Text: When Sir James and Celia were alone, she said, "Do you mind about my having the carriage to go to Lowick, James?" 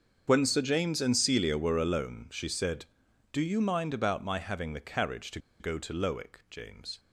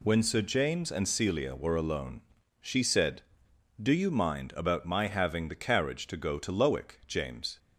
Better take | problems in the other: second | starts louder than the rest; until 1.2 s; 7 dB // pauses between "to" and "go"; slight; at 5.3 s; 0.21 s long

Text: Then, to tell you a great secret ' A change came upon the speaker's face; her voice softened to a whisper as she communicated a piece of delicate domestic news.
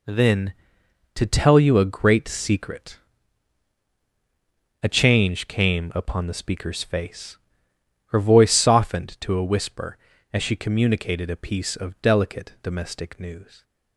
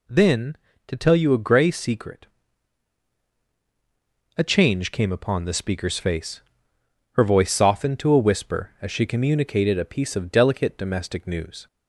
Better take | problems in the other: first | says "grey" for "great"; at 1.3 s

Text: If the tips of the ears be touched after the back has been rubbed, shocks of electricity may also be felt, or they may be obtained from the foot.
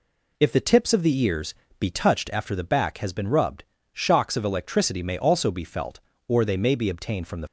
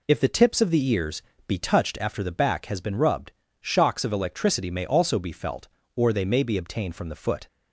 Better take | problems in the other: second | pauses between "ears" and "be"; slight; at 1.5 s; 0.24 s long; slight in the second // stops before "foot"; at 7.4 s

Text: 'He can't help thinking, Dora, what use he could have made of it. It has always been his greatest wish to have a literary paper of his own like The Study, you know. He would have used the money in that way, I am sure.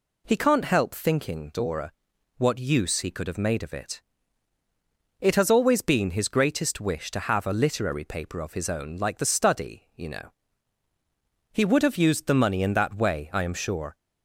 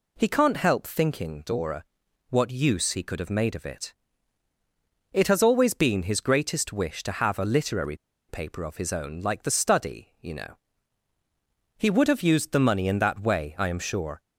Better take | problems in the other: first | pauses between "literary" and "paper"; slight; at 7.9 s; 0.31 s long

